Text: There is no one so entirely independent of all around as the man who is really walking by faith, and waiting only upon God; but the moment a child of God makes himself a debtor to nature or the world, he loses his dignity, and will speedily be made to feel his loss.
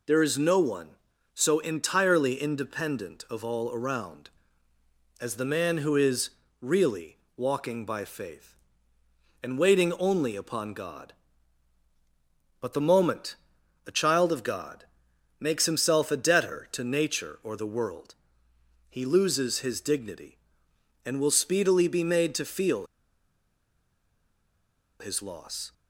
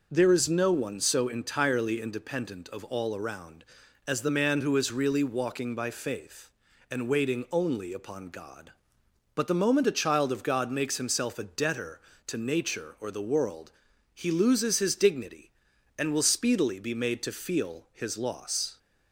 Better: second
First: pauses between "is" and "really"; slight; at 6.2 s; 0.30 s long // pauses between "really" and "walking"; slight; at 7.1 s; 0.18 s long // pauses between "moment" and "a"; noticeable; at 13.3 s; 0.50 s long // pauses between "God" and "makes"; noticeable; at 14.8 s; 0.54 s long // pauses between "feel" and "his"; strong; at 22.8 s; 2.1 s long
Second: none

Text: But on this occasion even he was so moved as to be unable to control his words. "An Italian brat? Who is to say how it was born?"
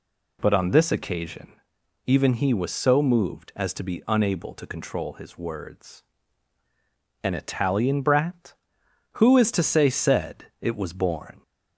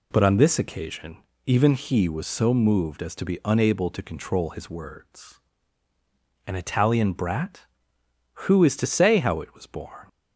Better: second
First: pauses between "occasion" and "even"; noticeable; at 1.5 s; 0.54 s long // says "said" for "how"; at 9.8 s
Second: pauses between "occasion" and "even"; slight; at 1.1 s; 0.26 s long

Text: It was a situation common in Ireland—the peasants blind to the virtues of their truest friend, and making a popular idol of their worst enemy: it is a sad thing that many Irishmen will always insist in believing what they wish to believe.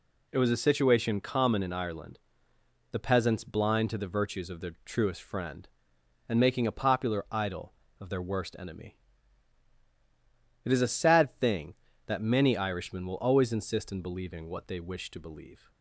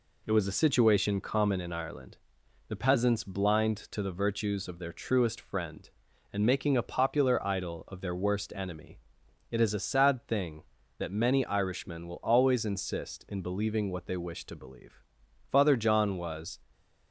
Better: first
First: none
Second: goes on to say "Father John was"; noticeable; from 15.4 s on; 1.0 s long

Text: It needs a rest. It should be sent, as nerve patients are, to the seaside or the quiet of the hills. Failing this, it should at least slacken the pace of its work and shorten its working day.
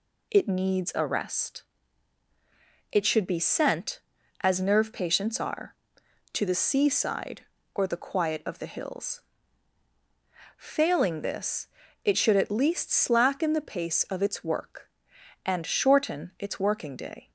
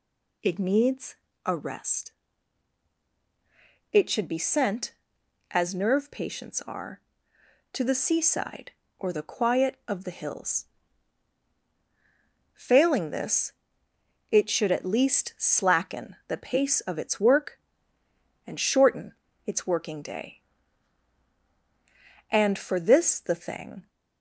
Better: first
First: none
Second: pauses between "needs" and "a"; slight; at 1.1 s; 0.30 s long // pauses between "shorten" and "its"; slight; at 19.1 s; 0.32 s long // goes on to say "And for this the thing"; from 22.2 s on; 1.5 s long

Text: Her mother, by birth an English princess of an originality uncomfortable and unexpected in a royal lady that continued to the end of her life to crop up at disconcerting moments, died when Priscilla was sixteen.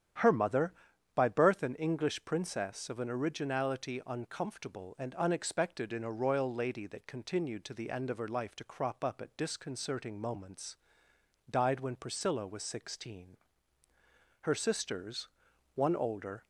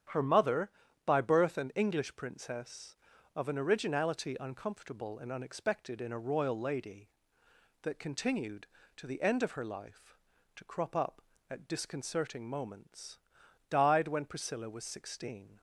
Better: second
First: starts louder than the rest; strong; until 1.6 s; 9.5 dB // goes on to say "Her sisters one older"; strong; from 14.4 s on; 2.0 s long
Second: starts louder than the rest; strong; until 1.4 s; 9 dB

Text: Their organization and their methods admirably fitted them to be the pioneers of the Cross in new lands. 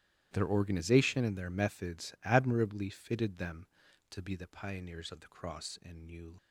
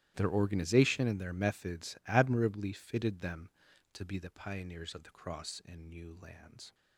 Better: second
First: starts louder than the rest; strong; until 1.3 s; 13 dB // stops before "lands"; at 6.3 s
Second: starts louder than the rest; strong; until 1.1 s; 13.5 dB

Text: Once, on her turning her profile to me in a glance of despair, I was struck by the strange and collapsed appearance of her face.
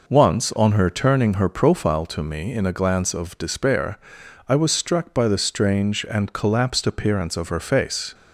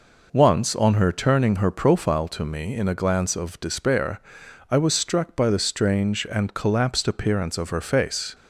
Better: neither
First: none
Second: none

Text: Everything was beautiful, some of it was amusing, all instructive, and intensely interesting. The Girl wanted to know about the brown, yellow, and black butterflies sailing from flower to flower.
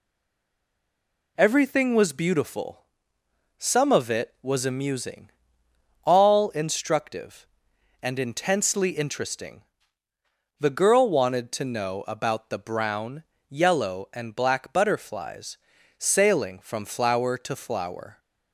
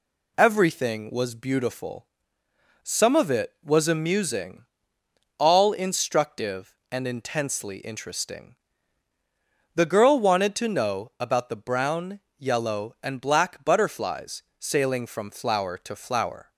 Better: second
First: stays silent before the first word; noticeable; until 1.3 s; 1.3 s long // pauses between "butterflies" and "sailing"; at 15.5 s; 0.40 s long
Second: pauses between "butterflies" and "sailing"; slight; at 14.4 s; 0.16 s long

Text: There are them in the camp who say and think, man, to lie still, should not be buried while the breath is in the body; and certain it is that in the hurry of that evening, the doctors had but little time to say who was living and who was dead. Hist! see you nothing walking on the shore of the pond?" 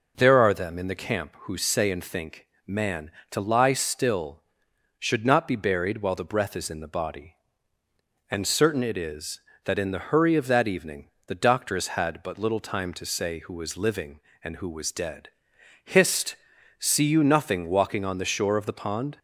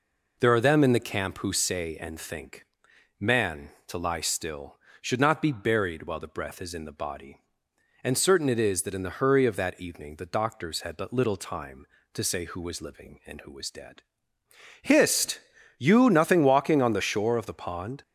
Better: first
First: none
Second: skips "see"; at 15.5 s

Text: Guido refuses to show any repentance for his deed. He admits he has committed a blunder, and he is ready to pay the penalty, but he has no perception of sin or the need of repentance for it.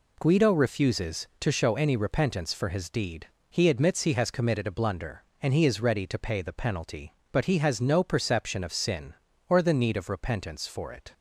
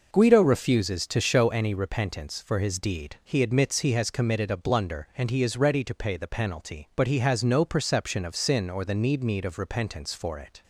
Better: first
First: none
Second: says "need" twice; at 9.2 s

